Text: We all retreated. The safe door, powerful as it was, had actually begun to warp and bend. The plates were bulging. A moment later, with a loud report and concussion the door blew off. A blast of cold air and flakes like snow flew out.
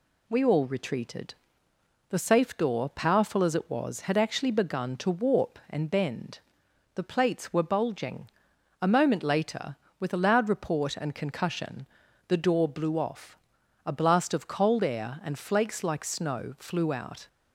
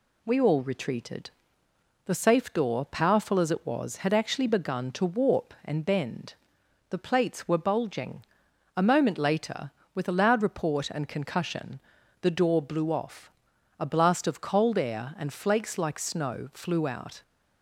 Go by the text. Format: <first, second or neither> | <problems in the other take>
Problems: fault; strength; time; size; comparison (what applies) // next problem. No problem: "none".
neither | pauses between "concussion" and "the"; the same in both